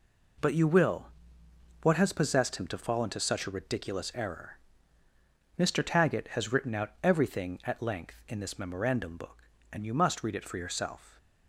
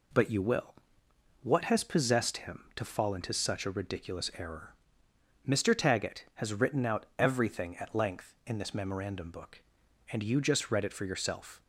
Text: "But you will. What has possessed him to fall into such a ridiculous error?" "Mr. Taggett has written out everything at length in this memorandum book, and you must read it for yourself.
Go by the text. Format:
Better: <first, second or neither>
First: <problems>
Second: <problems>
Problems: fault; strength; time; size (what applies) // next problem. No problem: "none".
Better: first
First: none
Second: says "just" for "must"; at 10.4 s